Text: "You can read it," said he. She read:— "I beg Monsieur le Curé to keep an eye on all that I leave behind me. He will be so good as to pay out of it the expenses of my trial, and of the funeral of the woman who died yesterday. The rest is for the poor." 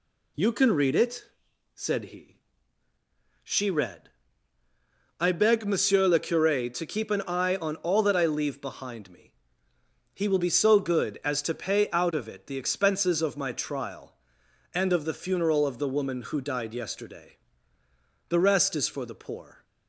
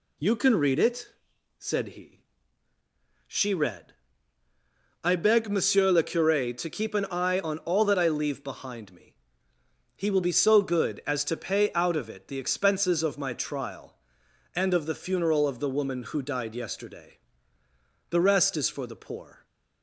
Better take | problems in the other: neither | none

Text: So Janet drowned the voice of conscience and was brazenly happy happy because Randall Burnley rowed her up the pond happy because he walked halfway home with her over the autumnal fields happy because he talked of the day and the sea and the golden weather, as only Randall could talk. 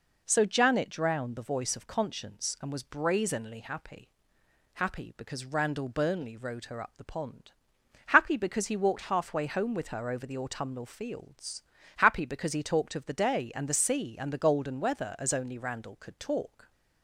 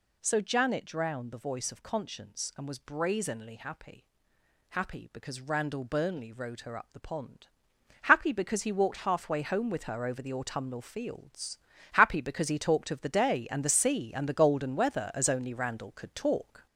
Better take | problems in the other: first | gets louder; noticeable; throughout; 4.5 dB // pauses between "happy" and "happy"; noticeable; at 4.0 s; 0.68 s long; noticeable in the first // pauses between "pond" and "happy"; noticeable; at 7.4 s; 0.54 s long; noticeable in the first // pauses between "fields" and "happy"; slight; at 11.5 s; 0.36 s long; slight in the first

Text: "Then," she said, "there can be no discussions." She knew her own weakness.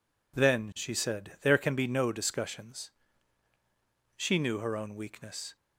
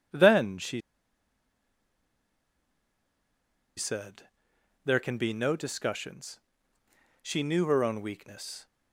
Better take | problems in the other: first | pauses between "she" and "said"; strong; at 0.7 s; 2.9 s long

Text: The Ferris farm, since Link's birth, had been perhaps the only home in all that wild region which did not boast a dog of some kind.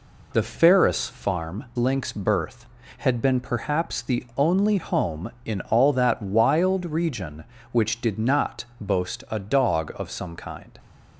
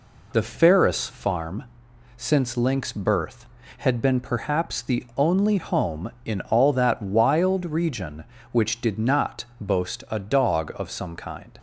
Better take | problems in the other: second | skips "since"; at 1.7 s

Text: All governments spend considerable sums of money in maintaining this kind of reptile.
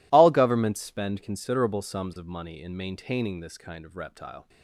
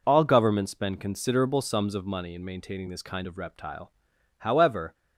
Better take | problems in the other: first | goes on to say "However"; from 4.3 s on; 0.56 s long

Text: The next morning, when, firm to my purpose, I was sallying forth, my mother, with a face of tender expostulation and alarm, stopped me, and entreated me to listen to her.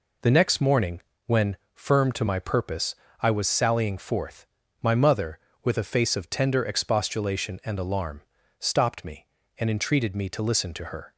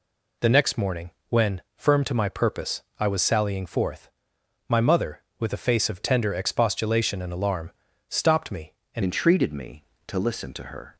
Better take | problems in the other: first | changes voice at "entreated"; from 9.0 s on; 1.9 s long

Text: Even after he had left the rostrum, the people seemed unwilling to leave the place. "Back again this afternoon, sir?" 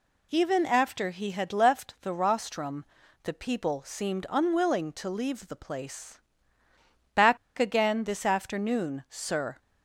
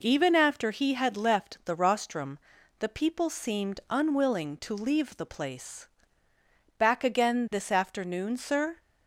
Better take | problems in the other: second | pauses between "Back" and "again"; slight; at 7.3 s; 0.21 s long

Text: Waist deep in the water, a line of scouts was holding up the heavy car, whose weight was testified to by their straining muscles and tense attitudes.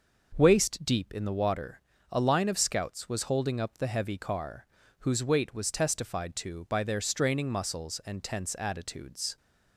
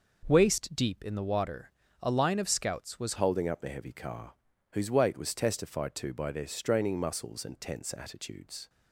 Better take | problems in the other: first | changes voice at "holding"; from 3.1 s on; 5.5 s long

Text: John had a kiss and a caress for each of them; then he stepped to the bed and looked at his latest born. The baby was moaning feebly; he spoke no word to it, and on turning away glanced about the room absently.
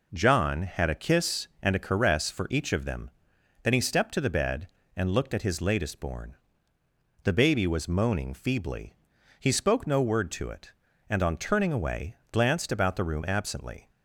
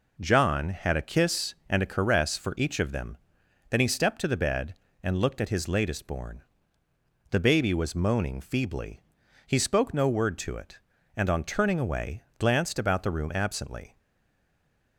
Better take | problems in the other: first | pauses between "away" and "glanced"; slight; at 12.2 s; 0.16 s long; slight in the first // stays silent after the last word; from 13.9 s on; 1.0 s long

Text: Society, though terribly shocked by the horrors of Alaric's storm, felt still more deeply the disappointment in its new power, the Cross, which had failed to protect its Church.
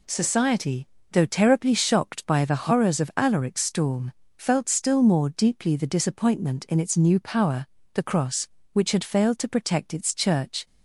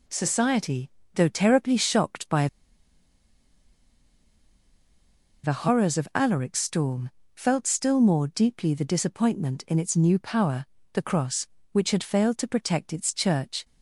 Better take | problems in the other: first | pauses between "by" and "the"; strong; at 2.4 s; 2.9 s long

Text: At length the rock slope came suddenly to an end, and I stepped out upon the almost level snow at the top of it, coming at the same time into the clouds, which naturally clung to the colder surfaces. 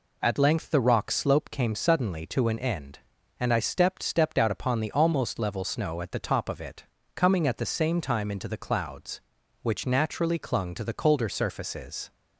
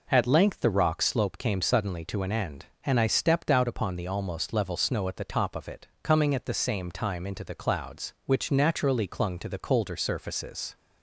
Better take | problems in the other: second | says "stepped" twice; at 4.0 s

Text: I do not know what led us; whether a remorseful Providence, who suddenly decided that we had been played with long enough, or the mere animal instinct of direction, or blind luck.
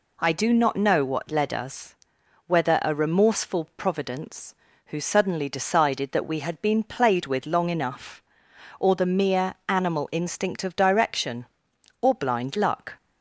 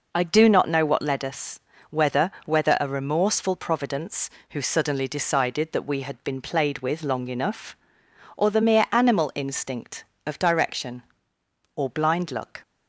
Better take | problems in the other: first | says "whether" twice; at 2.4 s

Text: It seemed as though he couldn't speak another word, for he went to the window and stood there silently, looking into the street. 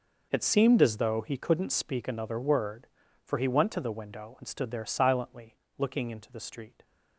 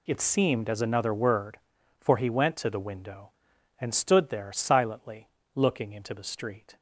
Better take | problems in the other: first | skips "though he couldn't speak"; at 0.8 s

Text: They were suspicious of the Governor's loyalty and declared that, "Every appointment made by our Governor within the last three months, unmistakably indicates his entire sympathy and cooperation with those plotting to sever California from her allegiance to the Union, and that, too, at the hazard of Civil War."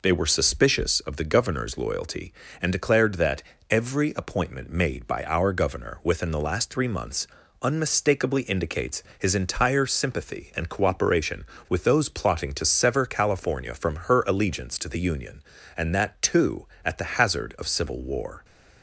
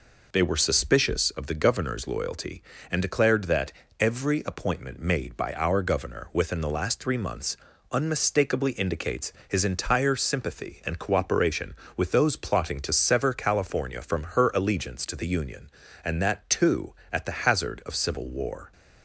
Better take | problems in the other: neither | pauses between "indicates" and "his"; slight; the same in both

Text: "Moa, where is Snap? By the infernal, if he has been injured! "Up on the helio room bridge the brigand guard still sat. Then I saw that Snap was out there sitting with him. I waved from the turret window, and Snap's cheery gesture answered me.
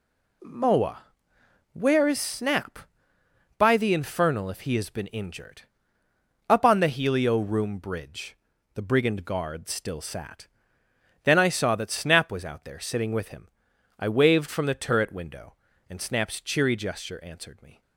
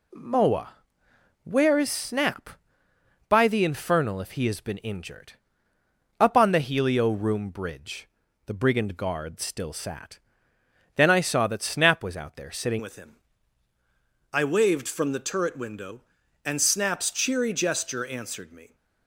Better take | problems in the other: first | pauses between "bridge" and "the"; at 8.0 s; 0.38 s long; also in the first // changes voice at "with"; from 12.7 s on; 6.0 s long

